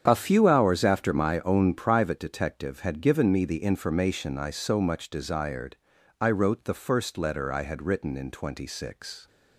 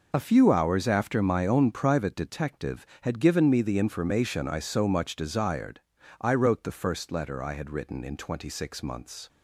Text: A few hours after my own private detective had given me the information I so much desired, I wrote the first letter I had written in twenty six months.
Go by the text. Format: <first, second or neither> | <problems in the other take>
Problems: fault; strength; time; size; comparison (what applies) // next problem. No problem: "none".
second | starts louder than the rest; strong; until 1.0 s; 7.5 dB // stops before "months"; at 9.2 s